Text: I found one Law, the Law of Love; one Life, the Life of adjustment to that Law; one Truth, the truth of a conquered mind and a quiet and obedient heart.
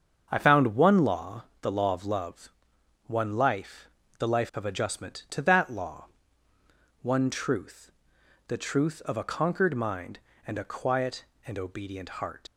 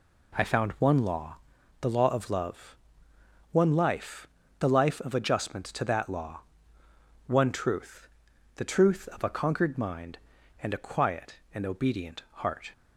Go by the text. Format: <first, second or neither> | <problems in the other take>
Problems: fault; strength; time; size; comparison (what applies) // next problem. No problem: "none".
second | starts louder than the rest; until 1.3 s; 7 dB // leaves "heart" unfinished; at 12.4 s; 70 ms